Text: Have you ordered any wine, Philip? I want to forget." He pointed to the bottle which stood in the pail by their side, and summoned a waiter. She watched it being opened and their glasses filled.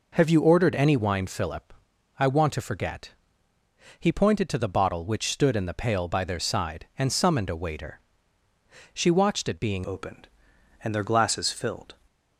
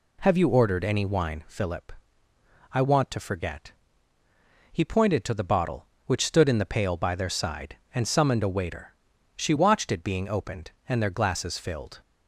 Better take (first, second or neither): second